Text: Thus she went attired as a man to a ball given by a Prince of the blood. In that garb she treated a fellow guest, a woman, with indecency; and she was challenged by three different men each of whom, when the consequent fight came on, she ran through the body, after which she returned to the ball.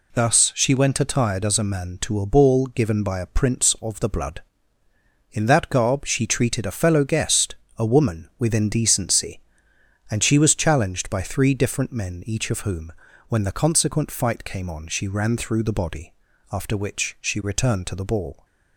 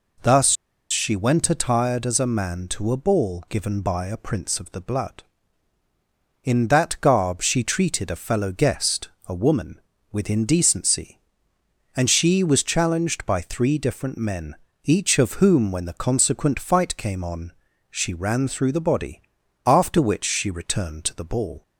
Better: first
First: none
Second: pauses between "Thus" and "she"; at 0.5 s; 0.37 s long // pauses between "men" and "each"; slight; at 14.5 s; 0.30 s long

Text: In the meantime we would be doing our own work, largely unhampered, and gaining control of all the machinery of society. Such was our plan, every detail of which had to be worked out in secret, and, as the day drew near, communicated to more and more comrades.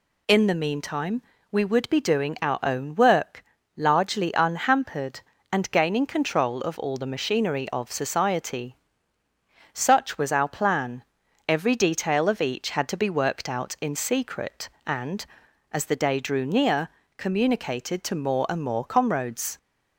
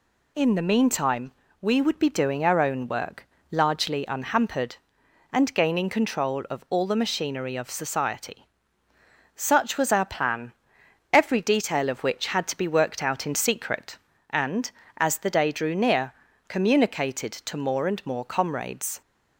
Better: second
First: pauses between "meantime" and "we"; slight; at 1.2 s; 0.30 s long // says "each" for "which"; at 12.3 s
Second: pauses between "meantime" and "we"; slight; at 1.3 s; 0.28 s long

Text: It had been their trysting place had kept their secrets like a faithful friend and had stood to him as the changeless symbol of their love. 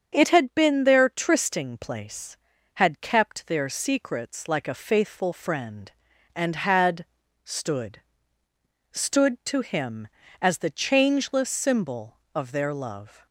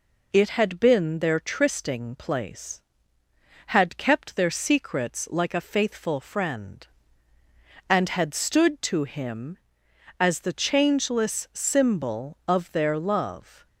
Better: second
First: starts louder than the rest; until 1.1 s; 7 dB // pauses between "had" and "stood"; at 7.0 s; 0.38 s long // says "stood" twice; at 8.9 s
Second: none

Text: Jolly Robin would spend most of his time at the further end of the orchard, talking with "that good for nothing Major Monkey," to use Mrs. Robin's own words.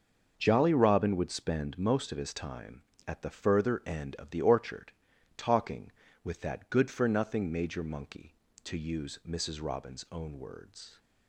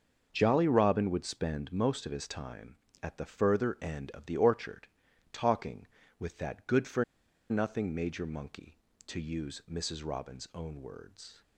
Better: first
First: starts louder than the rest; until 1.3 s; 6 dB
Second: starts louder than the rest; until 1.3 s; 6 dB // pauses between "for" and "nothing"; noticeable; at 7.0 s; 0.46 s long

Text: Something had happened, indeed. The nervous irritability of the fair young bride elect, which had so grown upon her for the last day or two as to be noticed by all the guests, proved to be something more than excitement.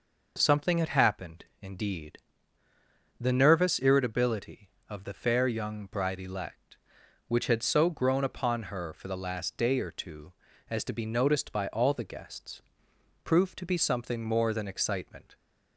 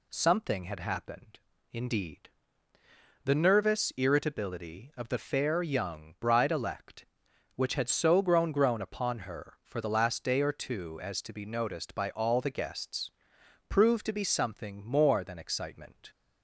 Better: first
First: none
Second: says "grown" twice; at 8.5 s

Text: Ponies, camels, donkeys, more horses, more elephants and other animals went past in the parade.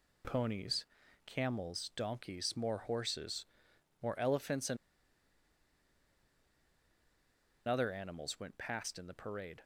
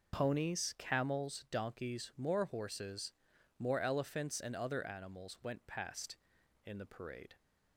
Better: second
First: pauses between "and" and "other"; strong; at 4.7 s; 2.9 s long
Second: none

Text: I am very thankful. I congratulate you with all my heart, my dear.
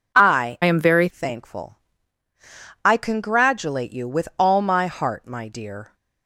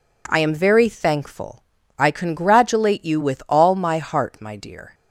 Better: second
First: changes voice from "am" to "very"; from 0.6 to 1.0 s; 0.4 s long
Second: none

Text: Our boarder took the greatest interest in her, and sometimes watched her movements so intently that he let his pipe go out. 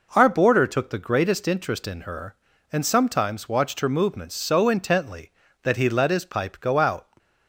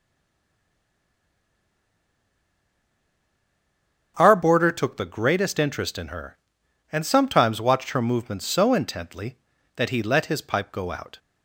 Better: first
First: none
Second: stays silent before the first word; strong; until 4.1 s; 4.1 s long // starts louder than the rest; strong; until 5.1 s; 7.5 dB

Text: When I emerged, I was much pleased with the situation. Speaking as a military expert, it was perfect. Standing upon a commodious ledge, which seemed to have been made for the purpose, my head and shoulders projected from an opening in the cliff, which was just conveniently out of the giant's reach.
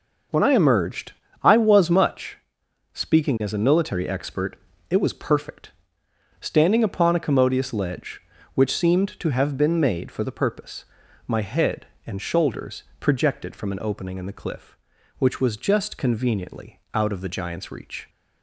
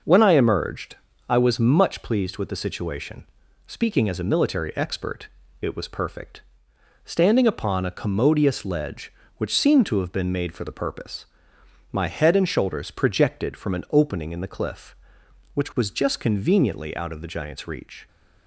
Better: second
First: skips "pleased with the situation"; at 2.6 s // pauses between "shoulders" and "projected"; slight; at 12.8 s; 0.16 s long // pauses between "conveniently" and "out"; slight; at 16.7 s; 0.16 s long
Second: none

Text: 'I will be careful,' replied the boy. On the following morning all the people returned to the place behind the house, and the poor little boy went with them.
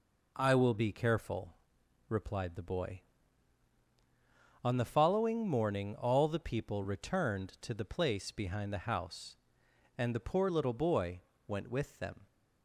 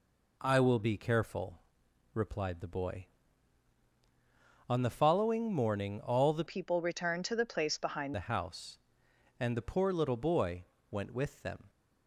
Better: first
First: pauses between "boy" and "went"; slight; at 11.2 s; 0.26 s long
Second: changes voice from "people" to "behind"; from 6.4 to 8.1 s; 1.7 s long // pauses between "boy" and "went"; slight; at 10.6 s; 0.26 s long

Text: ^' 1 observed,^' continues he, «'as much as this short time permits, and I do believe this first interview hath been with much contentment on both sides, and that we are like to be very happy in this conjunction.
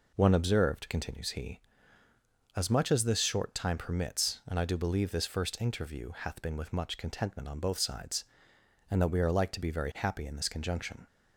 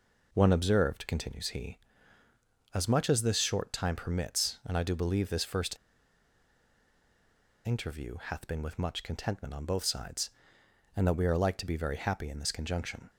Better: first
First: none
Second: pauses between "first" and "interview"; strong; at 5.7 s; 1.8 s long

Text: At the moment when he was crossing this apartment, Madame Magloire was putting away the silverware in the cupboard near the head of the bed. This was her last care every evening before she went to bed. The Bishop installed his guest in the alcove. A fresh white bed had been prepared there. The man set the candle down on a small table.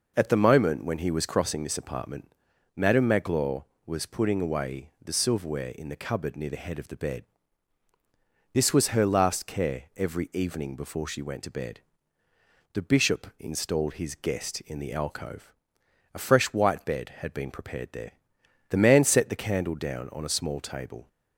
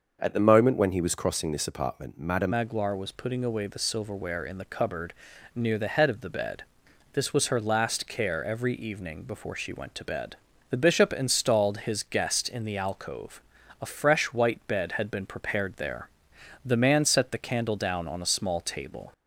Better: first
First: none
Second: starts louder than the rest; noticeable; until 1.2 s; 6 dB // changes voice at "Magloire"; from 2.5 s on; 16.6 s long // pauses between "cupboard" and "near"; at 5.1 s; 0.42 s long

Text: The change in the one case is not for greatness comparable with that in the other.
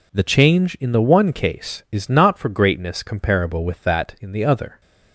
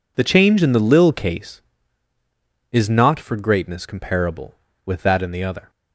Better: first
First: none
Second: says "lil" for "one"; at 0.7 s

